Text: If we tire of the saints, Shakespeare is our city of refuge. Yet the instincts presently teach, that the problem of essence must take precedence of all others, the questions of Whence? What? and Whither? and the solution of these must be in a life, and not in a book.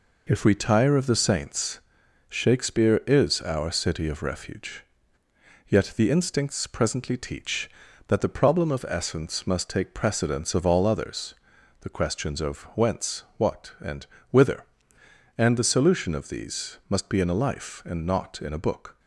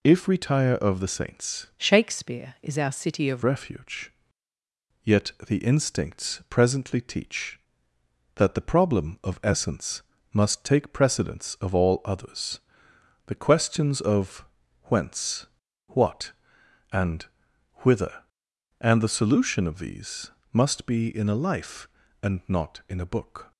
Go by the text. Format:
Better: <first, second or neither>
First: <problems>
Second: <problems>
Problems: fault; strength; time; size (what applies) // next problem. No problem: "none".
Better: first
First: pauses between "and" and "Whither"; slight; at 14.0 s; 0.24 s long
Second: changes voice from "Shakespeare" to "of"; from 1.7 to 3.4 s; 1.7 s long // pauses between "Yet" and "the"; slight; at 5.3 s; 0.16 s long // pauses between "essence" and "must"; slight; at 10.0 s; 0.30 s long // pauses between "of" and "Whence"; at 14.4 s; 0.38 s long // pauses between "and" and "Whither"; noticeable; at 17.2 s; 0.52 s long // pauses between "these" and "must"; slight; at 20.2 s; 0.24 s long